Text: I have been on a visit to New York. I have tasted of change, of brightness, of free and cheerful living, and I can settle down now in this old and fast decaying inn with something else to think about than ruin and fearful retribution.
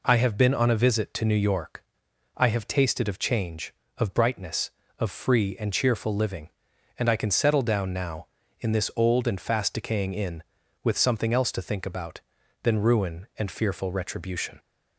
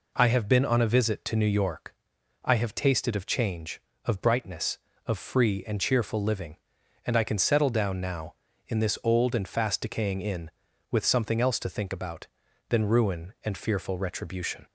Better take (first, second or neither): neither